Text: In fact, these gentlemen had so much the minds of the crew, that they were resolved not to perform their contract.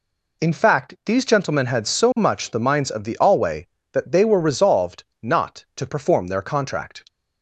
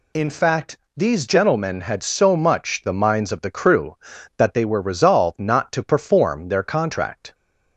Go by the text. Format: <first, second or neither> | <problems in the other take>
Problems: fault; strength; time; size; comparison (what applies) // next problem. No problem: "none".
second | says "alway" for "crew"; at 3.1 s // pauses between "resolved" and "not"; slight; at 5.0 s; 0.16 s long